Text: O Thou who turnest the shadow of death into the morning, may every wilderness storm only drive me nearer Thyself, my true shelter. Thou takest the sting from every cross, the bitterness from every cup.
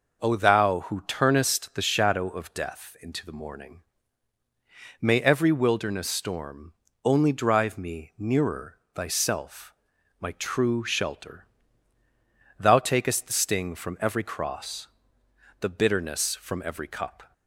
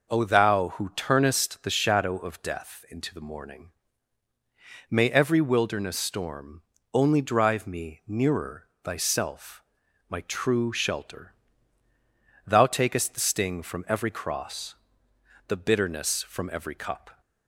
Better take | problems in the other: neither | pauses between "storm" and "only"; slight; the same in both // pauses between "nearer" and "Thyself"; slight; the same in both

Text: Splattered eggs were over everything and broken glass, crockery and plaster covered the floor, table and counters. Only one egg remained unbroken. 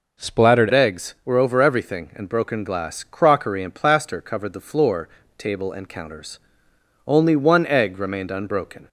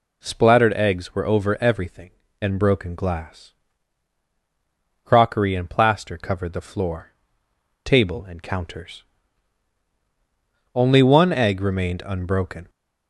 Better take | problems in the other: second | changes voice at "eggs"; from 0.7 s on; 8.1 s long

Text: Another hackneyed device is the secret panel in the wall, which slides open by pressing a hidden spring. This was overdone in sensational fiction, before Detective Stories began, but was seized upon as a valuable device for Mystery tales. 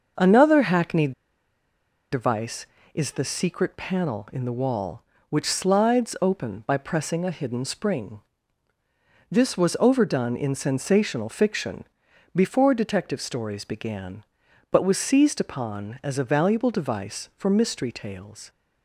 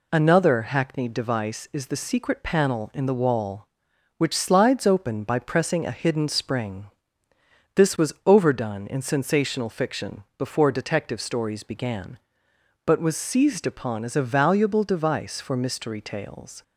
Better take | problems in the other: second | starts louder than the rest; noticeable; until 2.1 s; 6 dB // pauses between "hackneyed" and "device"; at 1.1 s; 1.0 s long

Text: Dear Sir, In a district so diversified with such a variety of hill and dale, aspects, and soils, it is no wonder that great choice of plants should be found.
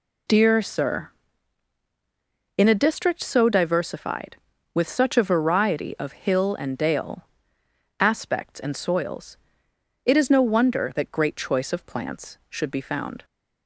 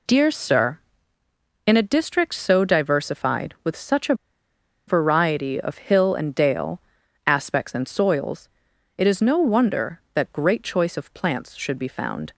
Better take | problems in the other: first | pauses between "a" and "variety"; noticeable; at 4.1 s; 0.73 s long

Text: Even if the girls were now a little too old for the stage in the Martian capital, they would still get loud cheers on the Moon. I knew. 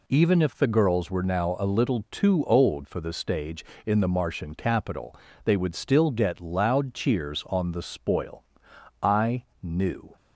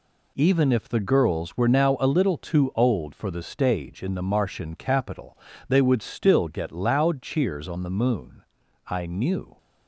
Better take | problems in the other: second | says "Spoil" for "Moon"; at 7.8 s // pauses between "I" and "knew"; slight; at 9.4 s; 0.18 s long

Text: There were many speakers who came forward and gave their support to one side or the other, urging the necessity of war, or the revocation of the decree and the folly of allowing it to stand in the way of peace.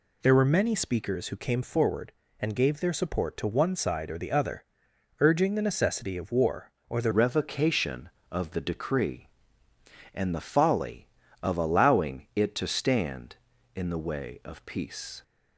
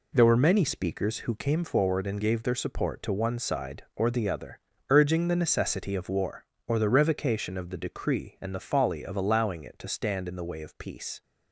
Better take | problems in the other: second | changes voice at "revocation"; from 7.1 s on; 8.1 s long

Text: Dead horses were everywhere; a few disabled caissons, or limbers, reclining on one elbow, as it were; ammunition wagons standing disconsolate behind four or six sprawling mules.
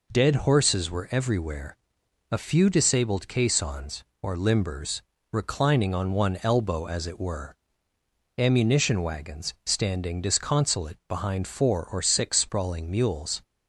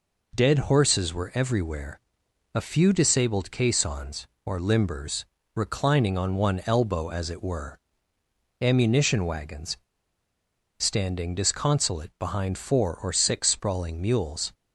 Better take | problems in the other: first | pauses between "wagons" and "standing"; at 9.7 s; 1.0 s long

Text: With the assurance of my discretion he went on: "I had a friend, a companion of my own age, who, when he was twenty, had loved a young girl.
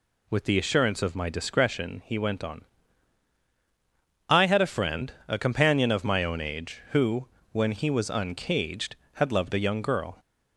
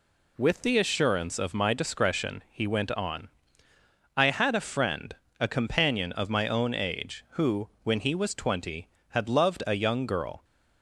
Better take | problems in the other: second | says "uncaged" for "twenty"; at 8.0 s

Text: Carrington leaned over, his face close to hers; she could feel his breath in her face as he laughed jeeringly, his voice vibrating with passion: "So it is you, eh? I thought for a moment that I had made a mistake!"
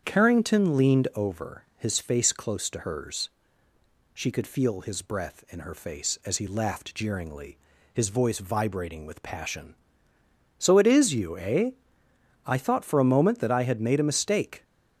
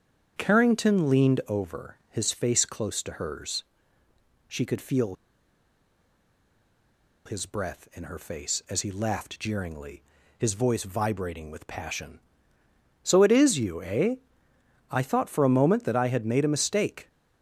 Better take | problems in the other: first | starts louder than the rest; strong; until 1.3 s; 8 dB; strong in the first // pauses between "feel" and "his"; strong; at 5.1 s; 2.1 s long

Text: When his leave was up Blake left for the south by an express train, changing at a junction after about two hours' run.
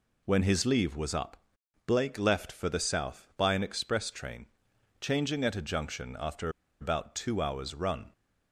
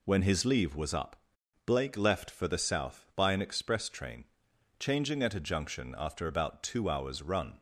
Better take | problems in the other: second | pauses between "up" and "Blake"; noticeable; at 1.3 s; 0.50 s long; noticeable in the second // pauses between "after" and "about"; slight; at 6.4 s; 0.32 s long

